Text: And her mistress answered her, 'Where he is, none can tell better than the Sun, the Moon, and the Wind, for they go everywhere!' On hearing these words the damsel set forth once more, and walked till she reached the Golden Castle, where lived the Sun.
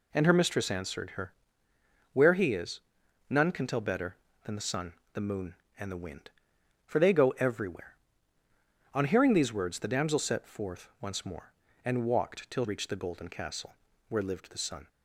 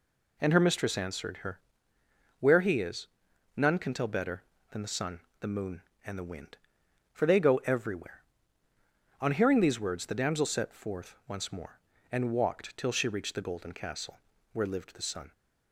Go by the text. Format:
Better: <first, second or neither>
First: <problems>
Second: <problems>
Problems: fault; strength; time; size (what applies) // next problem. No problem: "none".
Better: second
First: skips "she"; at 12.6 s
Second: none